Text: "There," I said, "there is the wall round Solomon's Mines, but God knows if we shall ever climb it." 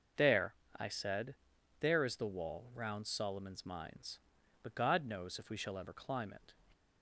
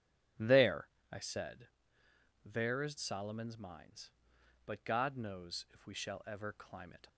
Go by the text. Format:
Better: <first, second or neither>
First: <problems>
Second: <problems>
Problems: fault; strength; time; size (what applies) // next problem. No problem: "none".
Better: first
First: none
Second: starts louder than the rest; strong; until 1.5 s; 9 dB // skips "the wall round"; at 2.9 s